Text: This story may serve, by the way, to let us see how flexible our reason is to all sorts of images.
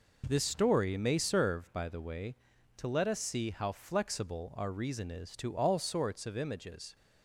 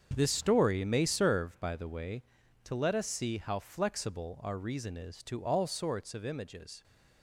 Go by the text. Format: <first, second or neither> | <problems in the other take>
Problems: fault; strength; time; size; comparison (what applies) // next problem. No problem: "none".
first | gets quieter; strong; throughout; 11 dB